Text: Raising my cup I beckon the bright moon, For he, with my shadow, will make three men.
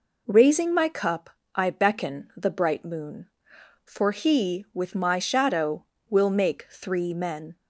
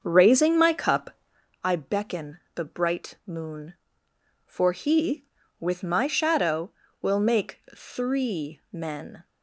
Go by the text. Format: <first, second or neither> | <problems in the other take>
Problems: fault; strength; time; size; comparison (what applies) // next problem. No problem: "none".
first | starts louder than the rest; until 1.5 s; 6.5 dB // pauses between "cup" and "I"; noticeable; at 1.1 s; 0.52 s long; slight in the first // pauses between "beckon" and "the"; slight; at 2.3 s; 0.16 s long // pauses between "make" and "three"; slight; at 7.5 s; 0.16 s long